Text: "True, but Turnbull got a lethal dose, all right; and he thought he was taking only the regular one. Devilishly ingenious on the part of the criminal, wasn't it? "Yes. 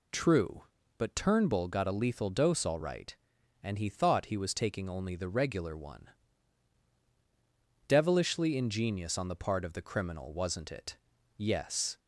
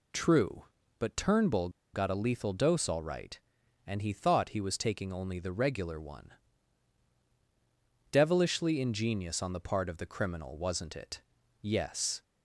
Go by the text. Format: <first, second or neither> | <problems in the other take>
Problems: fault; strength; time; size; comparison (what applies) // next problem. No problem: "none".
first | pauses between "Turnbull" and "got"; slight; at 1.6 s; 0.24 s long